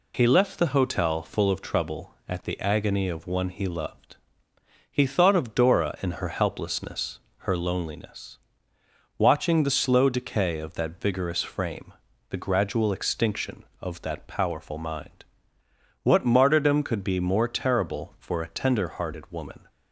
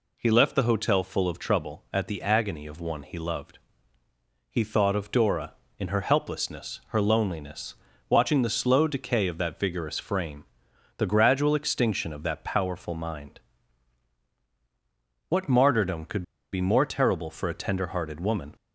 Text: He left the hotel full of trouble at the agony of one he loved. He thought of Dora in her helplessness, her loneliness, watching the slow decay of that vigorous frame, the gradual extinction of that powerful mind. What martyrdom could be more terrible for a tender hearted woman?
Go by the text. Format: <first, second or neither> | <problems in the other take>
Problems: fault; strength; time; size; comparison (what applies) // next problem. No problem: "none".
first | pauses between "could" and "be"; slight; at 16.2 s; 0.29 s long